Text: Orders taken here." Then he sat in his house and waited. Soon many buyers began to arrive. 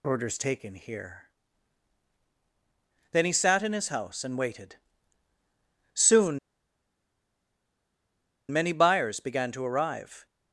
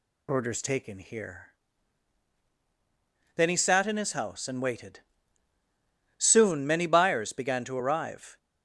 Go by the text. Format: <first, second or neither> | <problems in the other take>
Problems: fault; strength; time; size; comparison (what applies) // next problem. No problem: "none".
second | pauses between "Soon" and "many"; strong; at 6.3 s; 2.1 s long